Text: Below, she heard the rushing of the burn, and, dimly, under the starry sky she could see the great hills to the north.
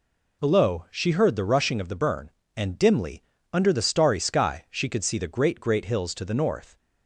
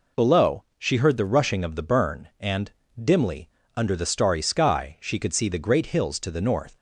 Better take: second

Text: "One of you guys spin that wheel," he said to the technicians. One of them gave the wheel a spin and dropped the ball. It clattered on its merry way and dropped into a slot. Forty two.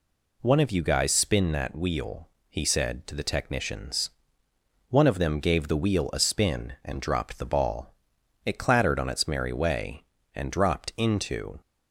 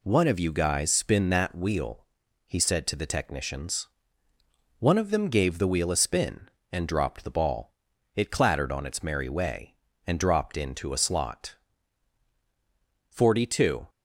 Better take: second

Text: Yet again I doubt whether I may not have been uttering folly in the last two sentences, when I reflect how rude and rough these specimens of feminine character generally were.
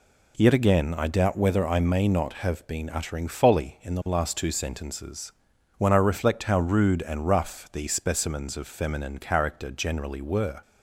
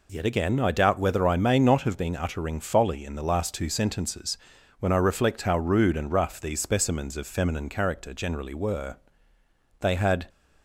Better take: first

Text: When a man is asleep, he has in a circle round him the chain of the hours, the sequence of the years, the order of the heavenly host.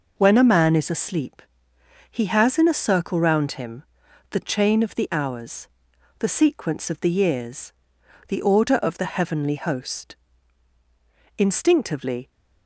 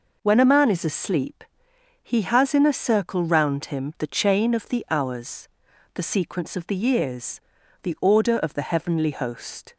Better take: second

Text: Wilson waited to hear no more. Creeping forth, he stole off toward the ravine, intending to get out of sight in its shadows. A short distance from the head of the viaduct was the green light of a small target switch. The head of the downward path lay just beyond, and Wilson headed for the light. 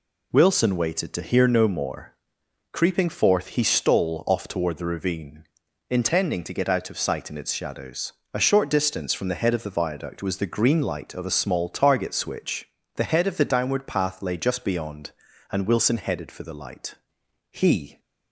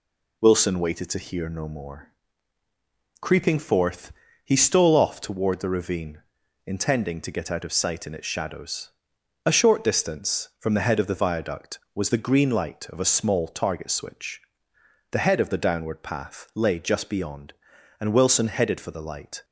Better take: second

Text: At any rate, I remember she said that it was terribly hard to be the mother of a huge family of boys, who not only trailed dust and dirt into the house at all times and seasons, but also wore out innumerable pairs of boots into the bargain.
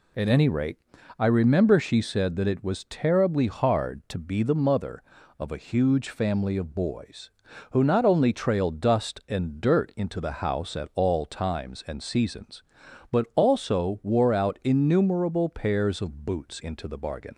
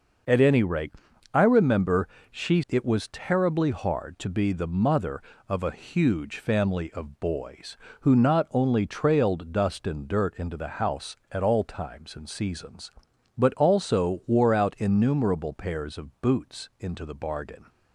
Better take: first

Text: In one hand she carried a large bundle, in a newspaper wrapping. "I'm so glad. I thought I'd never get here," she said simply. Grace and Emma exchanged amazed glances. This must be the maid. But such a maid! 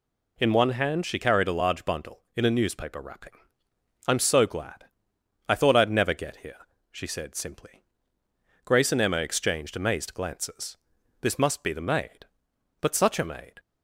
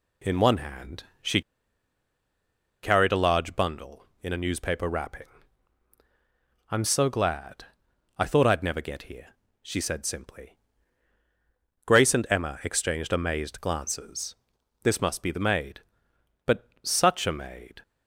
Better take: first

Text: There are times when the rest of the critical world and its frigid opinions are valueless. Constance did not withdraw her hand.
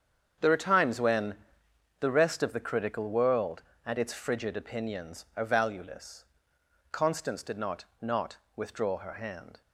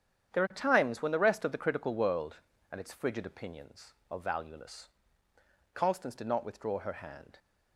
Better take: second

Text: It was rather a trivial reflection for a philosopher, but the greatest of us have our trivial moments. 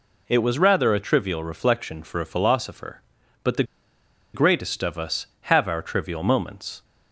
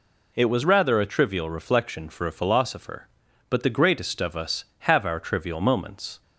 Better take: second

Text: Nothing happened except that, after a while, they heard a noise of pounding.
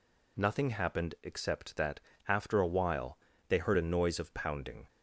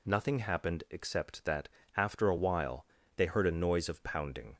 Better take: neither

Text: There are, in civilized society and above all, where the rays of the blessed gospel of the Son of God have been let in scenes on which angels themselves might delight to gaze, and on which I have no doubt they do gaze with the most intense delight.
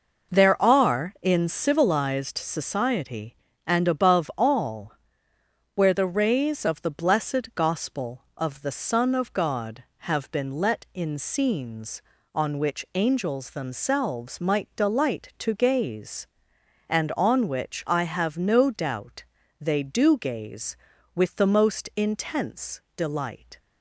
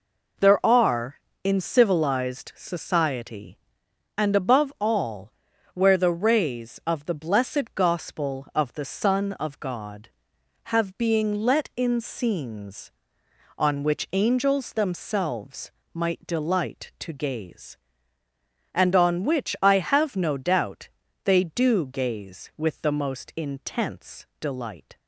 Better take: first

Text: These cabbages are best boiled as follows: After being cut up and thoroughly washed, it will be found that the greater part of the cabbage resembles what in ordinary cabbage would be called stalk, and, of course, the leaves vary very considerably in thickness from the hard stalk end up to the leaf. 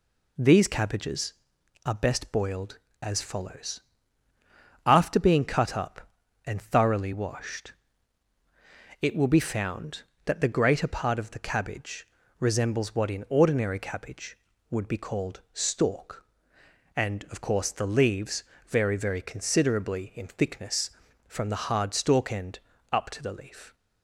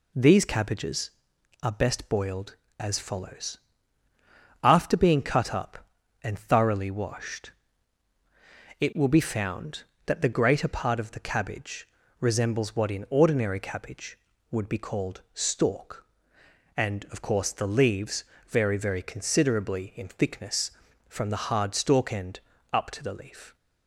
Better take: neither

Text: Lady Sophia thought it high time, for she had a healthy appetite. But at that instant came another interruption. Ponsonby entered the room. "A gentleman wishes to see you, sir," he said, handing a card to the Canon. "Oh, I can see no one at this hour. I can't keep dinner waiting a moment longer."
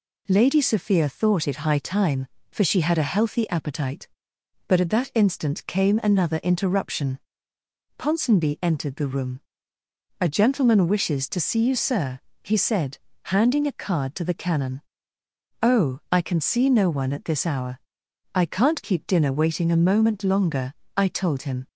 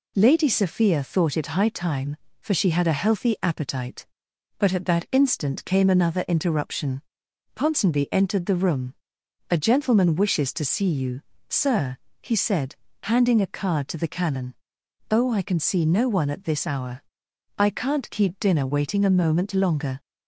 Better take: second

